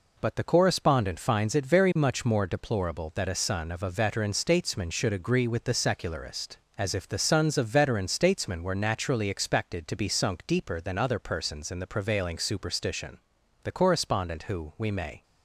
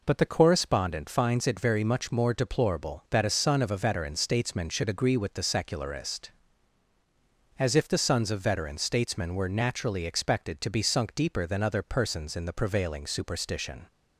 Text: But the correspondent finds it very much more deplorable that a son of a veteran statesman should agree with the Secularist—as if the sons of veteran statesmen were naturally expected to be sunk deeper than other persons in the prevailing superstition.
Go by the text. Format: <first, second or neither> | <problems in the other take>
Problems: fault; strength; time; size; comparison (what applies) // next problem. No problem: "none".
second | goes on to say "The correspondent who we may"; from 13.6 s on; 1.6 s long